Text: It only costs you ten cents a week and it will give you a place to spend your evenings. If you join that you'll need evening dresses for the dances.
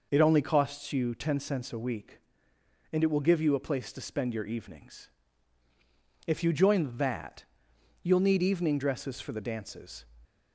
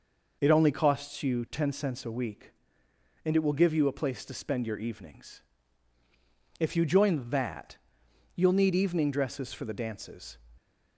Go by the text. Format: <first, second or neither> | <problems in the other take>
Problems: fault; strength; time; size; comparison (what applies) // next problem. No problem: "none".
neither | pauses between "that" and "you'll"; noticeable; the same in both